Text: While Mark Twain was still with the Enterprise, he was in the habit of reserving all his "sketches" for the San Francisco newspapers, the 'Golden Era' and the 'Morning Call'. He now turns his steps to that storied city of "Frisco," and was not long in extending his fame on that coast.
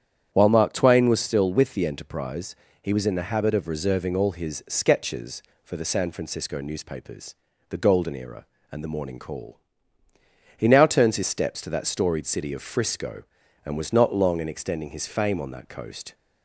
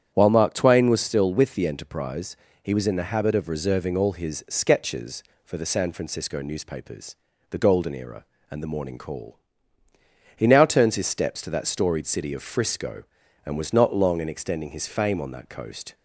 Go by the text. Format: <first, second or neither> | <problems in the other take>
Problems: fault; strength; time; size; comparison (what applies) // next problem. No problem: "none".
neither | starts louder than the rest; strong; the same in both